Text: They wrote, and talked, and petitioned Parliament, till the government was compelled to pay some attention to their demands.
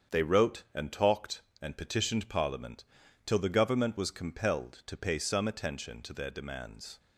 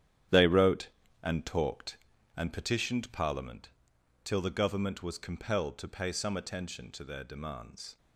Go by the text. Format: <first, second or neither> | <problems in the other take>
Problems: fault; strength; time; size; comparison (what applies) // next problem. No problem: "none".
first | gets quieter; strong; throughout; 10.5 dB // starts louder than the rest; strong; until 1.6 s; 10.5 dB; strong in the first